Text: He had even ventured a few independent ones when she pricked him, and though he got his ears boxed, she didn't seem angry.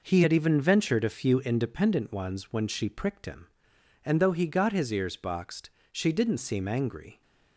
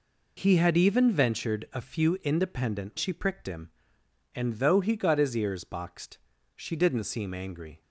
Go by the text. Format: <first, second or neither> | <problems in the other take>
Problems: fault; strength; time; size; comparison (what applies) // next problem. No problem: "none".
first | skips "ones when"; at 2.9 s